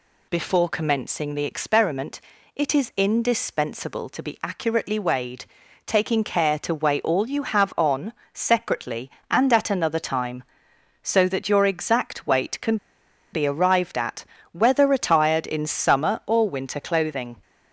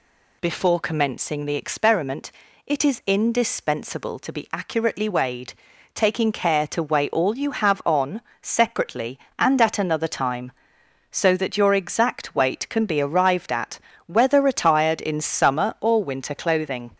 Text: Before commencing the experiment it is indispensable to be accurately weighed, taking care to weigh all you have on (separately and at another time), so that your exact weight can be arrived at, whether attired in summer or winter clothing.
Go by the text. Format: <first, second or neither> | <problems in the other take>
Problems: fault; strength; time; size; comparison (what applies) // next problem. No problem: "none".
second | pauses between "experiment" and "it"; slight; at 2.2 s; 0.34 s long; slight in the second // pauses between "can" and "be"; noticeable; at 12.7 s; 0.56 s long